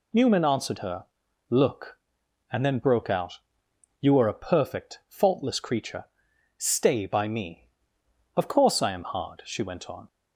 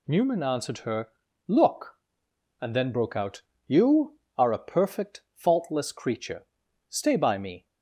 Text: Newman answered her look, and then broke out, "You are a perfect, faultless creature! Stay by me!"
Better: second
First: pauses between "her" and "look"; at 1.0 s; 0.44 s long // goes on to say "Of course I am hard she went on"; strong; from 8.3 s on; 1.7 s long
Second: pauses between "her" and "look"; at 1.0 s; 0.38 s long

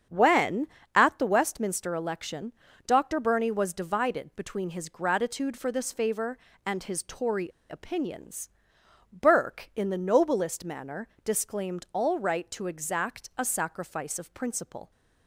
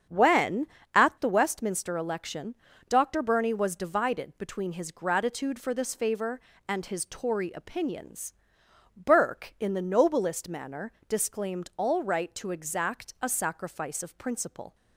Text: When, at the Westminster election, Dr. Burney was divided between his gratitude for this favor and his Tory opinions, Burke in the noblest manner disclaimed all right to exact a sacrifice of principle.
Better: second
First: starts louder than the rest; strong; until 1.3 s; 8 dB // pauses between "Tory" and "opinions"; slight; at 7.5 s; 0.20 s long // pauses between "manner" and "disclaimed"; slight; at 11.0 s; 0.16 s long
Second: starts louder than the rest; strong; until 1.4 s; 8 dB // pauses between "manner" and "disclaimed"; slight; at 10.9 s; 0.16 s long

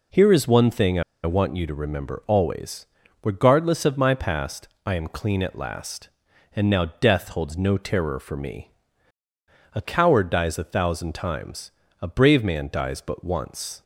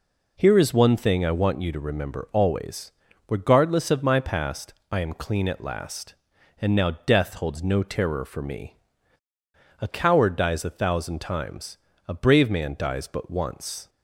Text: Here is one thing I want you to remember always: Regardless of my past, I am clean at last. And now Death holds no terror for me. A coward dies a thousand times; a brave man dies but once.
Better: second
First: pauses between "I" and "want"; slight; at 1.0 s; 0.21 s long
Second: none

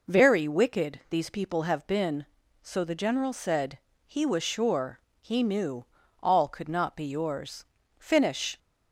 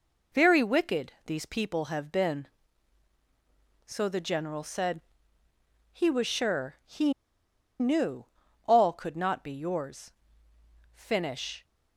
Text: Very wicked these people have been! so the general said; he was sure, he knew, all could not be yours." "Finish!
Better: first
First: none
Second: pauses between "wicked" and "these"; slight; at 1.1 s; 0.16 s long // pauses between "he" and "knew"; noticeable; at 7.1 s; 0.67 s long

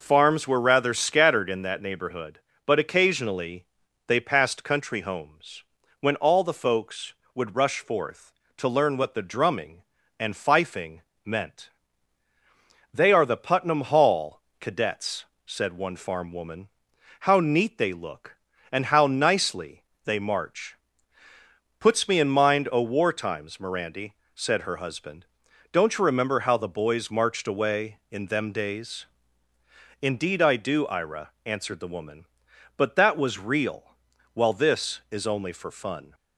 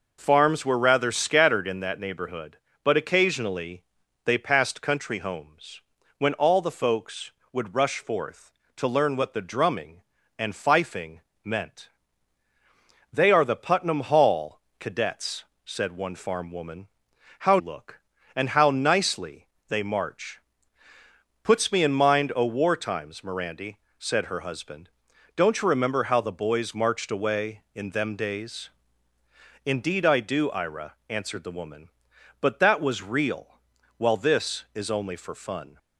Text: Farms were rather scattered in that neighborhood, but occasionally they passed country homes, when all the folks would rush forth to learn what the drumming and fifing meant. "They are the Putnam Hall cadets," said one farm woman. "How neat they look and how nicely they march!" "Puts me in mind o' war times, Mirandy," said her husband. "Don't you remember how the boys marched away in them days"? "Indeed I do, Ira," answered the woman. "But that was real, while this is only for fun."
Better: first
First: pauses between "occasionally" and "they"; at 3.6 s; 0.42 s long // pauses between "fifing" and "meant"; slight; at 11.0 s; 0.20 s long // pauses between "Hall" and "cadets"; slight; at 14.4 s; 0.18 s long // pauses between "nicely" and "they"; slight; at 19.8 s; 0.24 s long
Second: pauses between "occasionally" and "they"; at 3.8 s; 0.42 s long // pauses between "fifing" and "meant"; slight; at 11.2 s; 0.20 s long // pauses between "Hall" and "cadets"; slight; at 14.5 s; 0.18 s long // skips "neat they"; at 17.5 s // pauses between "nicely" and "they"; slight; at 19.4 s; 0.24 s long

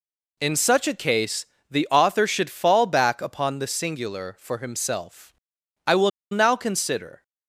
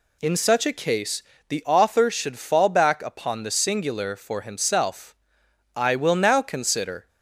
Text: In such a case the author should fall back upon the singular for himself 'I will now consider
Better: second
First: pauses between "case" and "the"; slight; at 1.4 s; 0.24 s long // pauses between "himself" and "I"; noticeable; at 5.3 s; 0.54 s long // pauses between "will" and "now"; slight; at 6.1 s; 0.22 s long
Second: pauses between "case" and "the"; slight; at 1.2 s; 0.24 s long // pauses between "himself" and "I"; noticeable; at 5.1 s; 0.62 s long

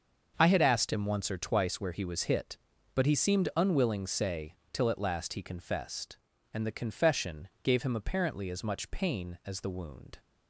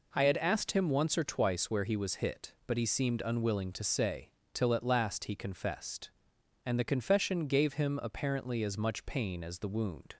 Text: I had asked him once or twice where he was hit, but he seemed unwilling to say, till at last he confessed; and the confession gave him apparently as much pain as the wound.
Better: second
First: starts louder than the rest; until 1.3 s; 6.5 dB // skips "to"; at 4.0 s // pauses between "confession" and "gave"; slight; at 7.4 s; 0.16 s long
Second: none

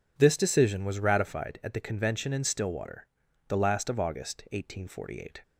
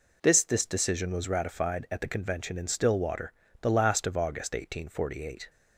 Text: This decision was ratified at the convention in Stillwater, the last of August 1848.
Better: first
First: none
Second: says "This" twice; at 0.4 s

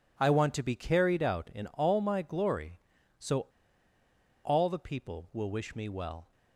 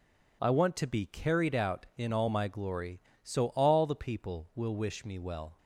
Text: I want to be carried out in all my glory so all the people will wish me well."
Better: second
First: pauses between "so" and "all"; at 3.4 s; 1.0 s long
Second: none

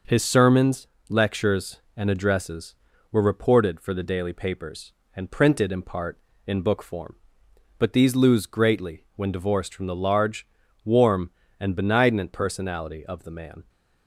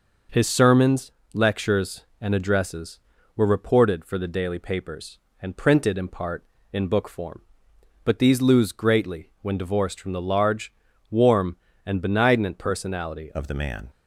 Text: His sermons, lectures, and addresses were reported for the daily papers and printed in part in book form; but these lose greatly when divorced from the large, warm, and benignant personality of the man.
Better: first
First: none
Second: changes voice at "of"; from 13.3 s on; 0.5 s long

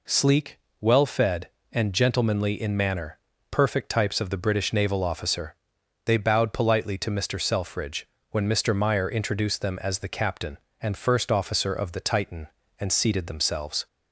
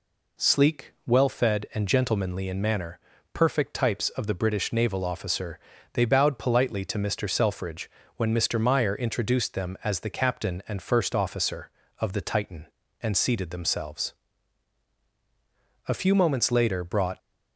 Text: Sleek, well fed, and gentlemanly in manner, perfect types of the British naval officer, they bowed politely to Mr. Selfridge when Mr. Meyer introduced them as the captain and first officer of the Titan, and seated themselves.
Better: first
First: pauses between "Selfridge" and "when"; slight; at 8.0 s; 0.24 s long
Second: pauses between "Selfridge" and "when"; slight; at 7.8 s; 0.28 s long // goes on to say "A few moments later brought"; noticeable; from 15.8 s on; 1.3 s long

